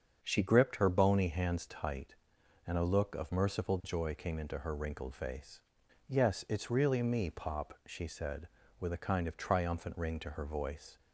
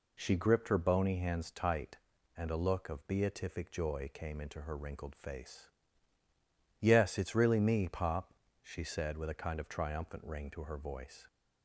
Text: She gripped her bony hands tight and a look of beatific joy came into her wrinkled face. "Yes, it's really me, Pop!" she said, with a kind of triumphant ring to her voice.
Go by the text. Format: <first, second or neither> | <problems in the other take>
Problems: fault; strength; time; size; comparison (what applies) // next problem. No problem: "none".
second | starts louder than the rest; strong; until 1.2 s; 7 dB // says "merciful" for "beatific"; at 3.3 s